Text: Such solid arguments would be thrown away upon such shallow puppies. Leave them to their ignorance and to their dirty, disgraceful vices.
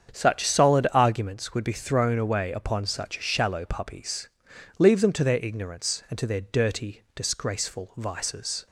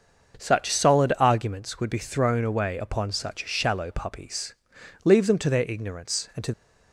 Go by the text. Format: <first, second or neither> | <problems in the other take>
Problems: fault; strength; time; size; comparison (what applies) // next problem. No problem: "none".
first | starts louder than the rest; until 1.4 s; 6.5 dB; strong in the first // stops before "their dirty disgraceful vices"; at 6.5 s